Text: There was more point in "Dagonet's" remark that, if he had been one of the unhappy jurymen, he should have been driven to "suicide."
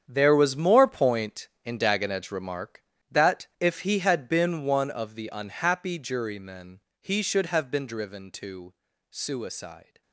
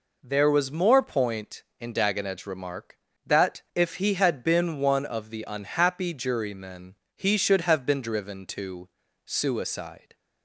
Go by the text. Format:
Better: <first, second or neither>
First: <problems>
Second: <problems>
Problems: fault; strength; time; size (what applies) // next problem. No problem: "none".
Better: second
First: gets quieter; strong; throughout; 13.5 dB // pauses between "to" and "suicide"; slight; at 8.7 s; 0.36 s long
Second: pauses between "to" and "suicide"; slight; at 8.8 s; 0.36 s long